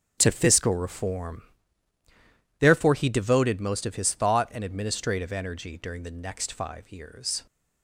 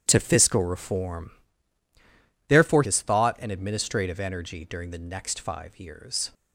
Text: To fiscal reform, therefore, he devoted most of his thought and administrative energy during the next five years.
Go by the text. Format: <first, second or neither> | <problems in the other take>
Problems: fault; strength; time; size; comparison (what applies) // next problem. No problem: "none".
first | starts louder than the rest; strong; until 1.0 s; 10.5 dB; strong in the first // skips "he devoted most of"; at 2.8 s